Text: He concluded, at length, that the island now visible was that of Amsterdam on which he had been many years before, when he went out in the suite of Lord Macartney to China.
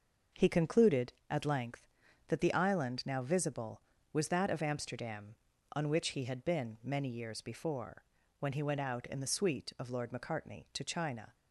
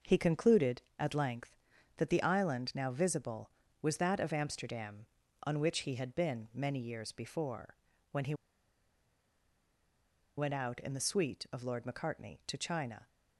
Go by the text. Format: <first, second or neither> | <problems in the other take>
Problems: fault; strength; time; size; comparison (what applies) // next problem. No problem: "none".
first | starts louder than the rest; noticeable; until 1.2 s; 6 dB; noticeable in the first // pauses between "he" and "went"; strong; at 8.3 s; 2.0 s long